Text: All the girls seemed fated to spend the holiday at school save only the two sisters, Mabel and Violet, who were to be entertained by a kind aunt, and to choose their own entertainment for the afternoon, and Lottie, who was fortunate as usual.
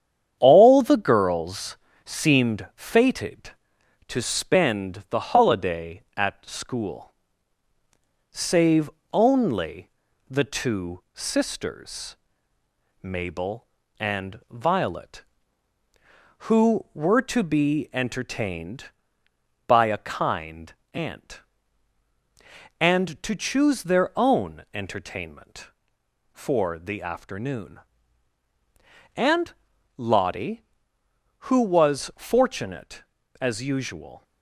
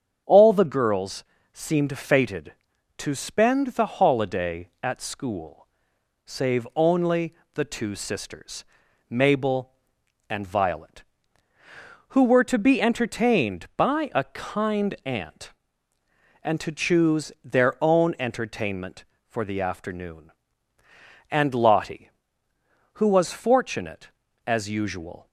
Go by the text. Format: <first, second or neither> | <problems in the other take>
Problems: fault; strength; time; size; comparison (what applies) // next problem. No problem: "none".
second | gets quieter; noticeable; throughout; 4.5 dB // starts louder than the rest; strong; until 1.3 s; 9 dB; strong in the second // pauses between "girls" and "seemed"; slight; at 1.7 s; 0.30 s long; slight in the second // pauses between "school" and "save"; at 7.1 s; 1.2 s long; noticeable in the second // pauses between "save" and "only"; slight; at 8.8 s; 0.22 s long // pauses between "only" and "the"; at 9.8 s; 0.40 s long; slight in the second // pauses between "kind" and "aunt"; slight; at 20.7 s; 0.22 s long // pauses between "and" and "Lottie"; at 29.5 s; 0.44 s long